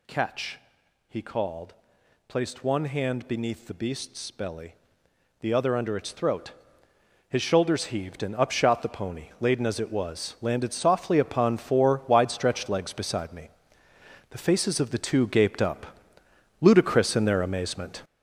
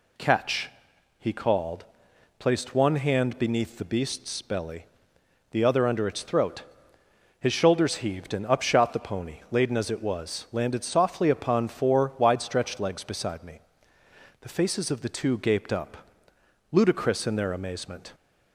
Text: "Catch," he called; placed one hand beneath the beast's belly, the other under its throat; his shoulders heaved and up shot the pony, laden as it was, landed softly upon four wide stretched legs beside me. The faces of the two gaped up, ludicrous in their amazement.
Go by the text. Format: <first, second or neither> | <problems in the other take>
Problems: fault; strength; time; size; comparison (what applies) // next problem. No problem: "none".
second | gets louder; strong; throughout; 8 dB